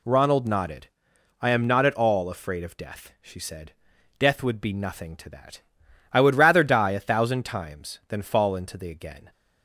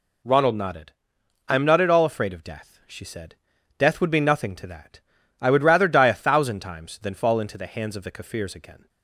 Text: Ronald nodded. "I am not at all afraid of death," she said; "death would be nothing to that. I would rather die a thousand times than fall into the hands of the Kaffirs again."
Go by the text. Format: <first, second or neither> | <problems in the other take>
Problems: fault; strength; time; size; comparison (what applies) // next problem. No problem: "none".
second | skips "hands of the Kaffirs"; at 8.9 s